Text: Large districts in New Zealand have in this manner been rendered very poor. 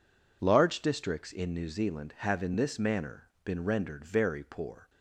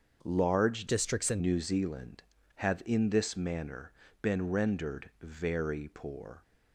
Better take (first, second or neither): first